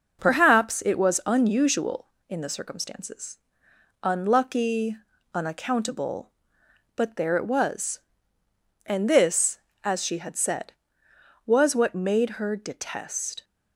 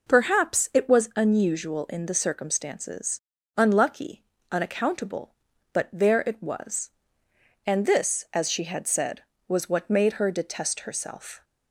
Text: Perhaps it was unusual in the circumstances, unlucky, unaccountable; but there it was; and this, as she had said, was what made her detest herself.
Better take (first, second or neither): second